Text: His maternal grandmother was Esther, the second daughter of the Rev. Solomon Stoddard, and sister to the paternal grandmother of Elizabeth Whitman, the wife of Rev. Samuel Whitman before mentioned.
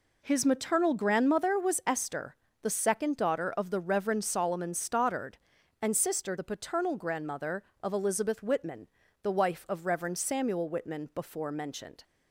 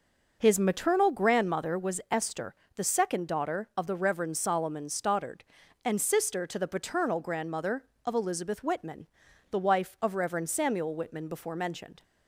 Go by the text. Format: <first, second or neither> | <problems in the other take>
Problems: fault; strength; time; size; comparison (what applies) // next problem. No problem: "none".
second | skips "to"; at 6.3 s